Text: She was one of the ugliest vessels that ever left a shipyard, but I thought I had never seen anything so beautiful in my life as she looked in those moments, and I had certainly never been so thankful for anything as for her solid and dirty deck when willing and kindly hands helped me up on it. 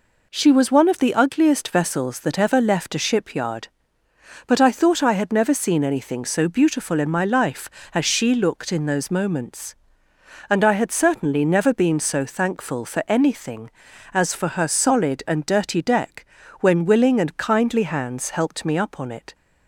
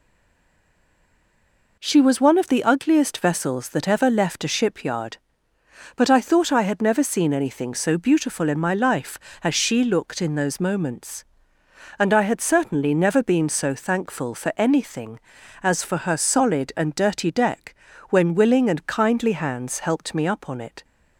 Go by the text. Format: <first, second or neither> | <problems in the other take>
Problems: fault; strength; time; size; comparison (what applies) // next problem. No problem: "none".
first | stays silent before the first word; noticeable; until 1.7 s; 1.7 s long // pauses between "deck" and "when"; slight; at 17.7 s; 0.34 s long; slight in the first